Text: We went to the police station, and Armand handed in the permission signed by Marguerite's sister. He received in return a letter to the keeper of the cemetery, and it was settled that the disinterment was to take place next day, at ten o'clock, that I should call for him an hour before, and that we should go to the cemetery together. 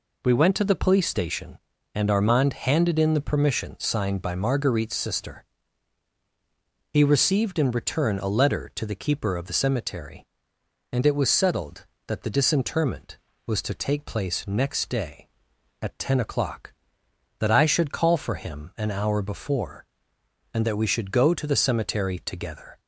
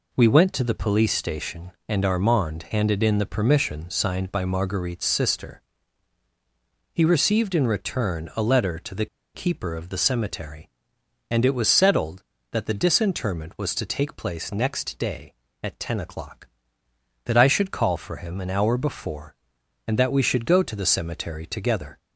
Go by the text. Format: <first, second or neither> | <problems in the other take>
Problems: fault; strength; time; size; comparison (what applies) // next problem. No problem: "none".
first | pauses between "the" and "keeper"; slight; at 9.0 s; 0.29 s long